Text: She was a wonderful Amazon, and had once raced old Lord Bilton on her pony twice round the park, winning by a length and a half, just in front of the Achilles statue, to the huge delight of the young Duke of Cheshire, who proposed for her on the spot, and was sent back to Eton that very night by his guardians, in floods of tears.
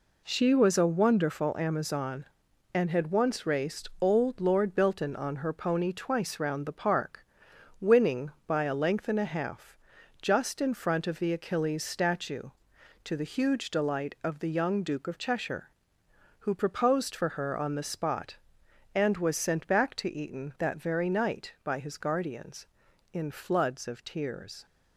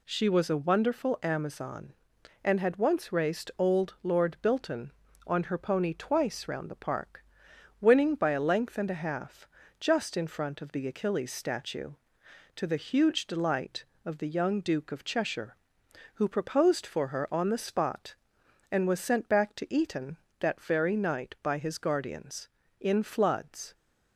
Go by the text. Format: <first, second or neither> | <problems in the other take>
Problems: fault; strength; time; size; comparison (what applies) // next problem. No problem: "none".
first | stops before "of tears"; at 23.7 s